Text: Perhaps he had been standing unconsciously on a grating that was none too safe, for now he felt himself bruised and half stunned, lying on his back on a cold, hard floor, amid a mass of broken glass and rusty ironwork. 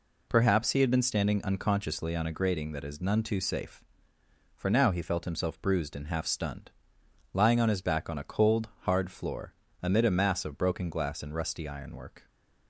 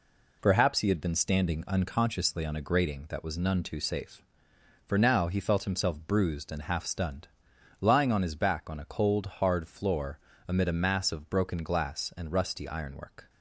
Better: second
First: says "is" for "was"; at 2.8 s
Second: none

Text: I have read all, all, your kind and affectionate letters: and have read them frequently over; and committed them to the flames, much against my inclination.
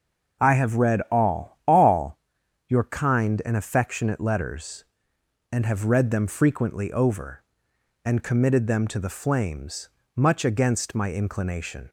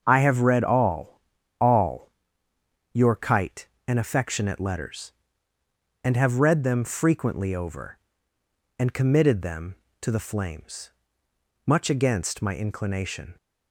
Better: first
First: starts louder than the rest; noticeable; until 1.5 s; 6 dB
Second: starts louder than the rest; until 1.0 s; 7 dB // says "kite" for "kind"; at 3.1 s

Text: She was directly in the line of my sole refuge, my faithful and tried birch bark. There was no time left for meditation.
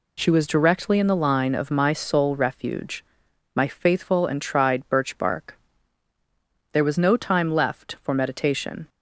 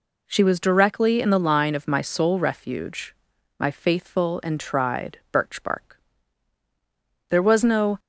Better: first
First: none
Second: stops before "time left for meditation"; at 7.9 s

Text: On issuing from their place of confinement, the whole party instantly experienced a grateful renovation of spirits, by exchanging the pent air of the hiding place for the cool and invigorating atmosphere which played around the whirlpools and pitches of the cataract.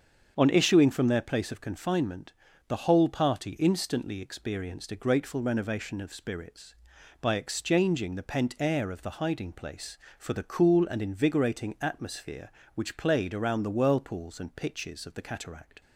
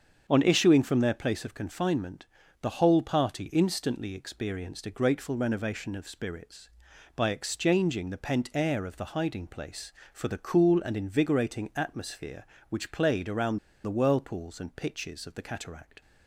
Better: first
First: starts louder than the rest; strong; until 1.3 s; 7.5 dB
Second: starts louder than the rest; strong; until 1.2 s; 7.5 dB // pauses between "around" and "the"; slight; at 13.5 s; 0.27 s long

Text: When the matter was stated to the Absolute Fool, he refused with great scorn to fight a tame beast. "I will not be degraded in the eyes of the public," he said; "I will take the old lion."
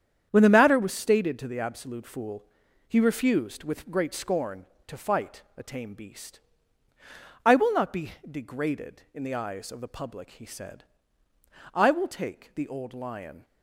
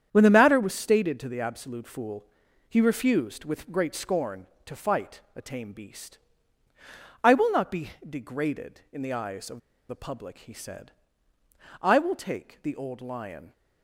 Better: first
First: starts louder than the rest; strong; until 1.3 s; 8.5 dB // pauses between "be" and "degraded"; slight; at 8.1 s; 0.16 s long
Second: starts louder than the rest; strong; until 1.1 s; 8.5 dB // pauses between "be" and "degraded"; slight; at 7.9 s; 0.16 s long // pauses between "of" and "the"; slight; at 9.5 s; 0.30 s long

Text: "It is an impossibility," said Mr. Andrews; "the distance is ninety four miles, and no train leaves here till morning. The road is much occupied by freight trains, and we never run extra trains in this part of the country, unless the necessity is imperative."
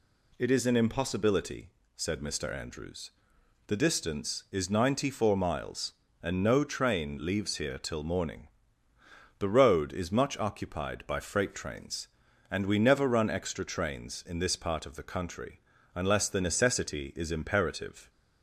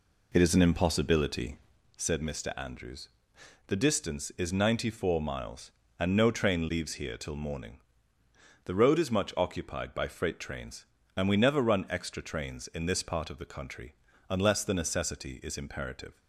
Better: first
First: none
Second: starts louder than the rest; slight; until 1.8 s; 3 dB

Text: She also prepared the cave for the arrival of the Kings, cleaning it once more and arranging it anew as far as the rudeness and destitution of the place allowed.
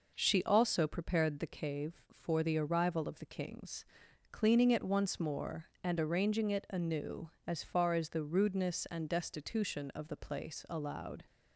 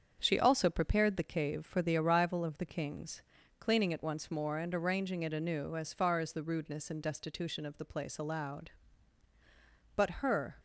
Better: first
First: none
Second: starts louder than the rest; strong; until 1.2 s; 7.5 dB // goes on to say "But her"; noticeable; from 9.9 s on; 0.64 s long

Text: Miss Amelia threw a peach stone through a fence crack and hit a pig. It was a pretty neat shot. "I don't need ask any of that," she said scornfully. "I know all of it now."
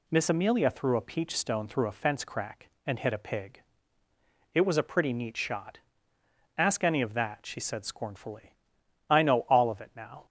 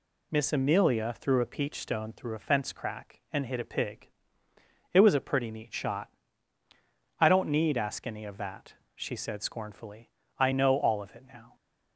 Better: second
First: skips "I don't need"; at 6.1 s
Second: none

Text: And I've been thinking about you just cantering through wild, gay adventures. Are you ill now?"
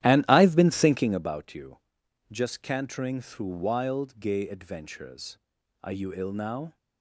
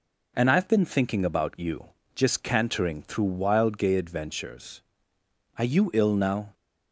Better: second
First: starts louder than the rest; strong; until 1.3 s; 12.5 dB // pauses between "you" and "just"; noticeable; at 1.7 s; 0.52 s long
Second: pauses between "you" and "just"; slight; at 1.8 s; 0.30 s long

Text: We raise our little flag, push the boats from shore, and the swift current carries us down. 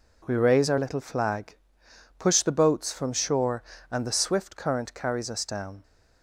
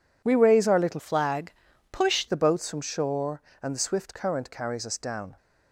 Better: first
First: none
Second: changes voice from "flag" to "push"; from 0.9 to 2.2 s; 1.3 s long

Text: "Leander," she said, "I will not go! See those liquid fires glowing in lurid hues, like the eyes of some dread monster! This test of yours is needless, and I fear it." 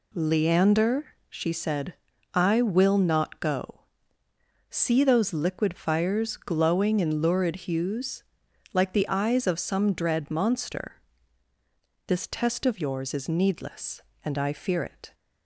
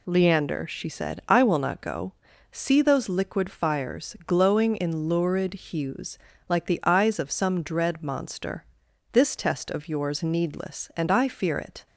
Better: first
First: none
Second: skips "is"; at 10.2 s

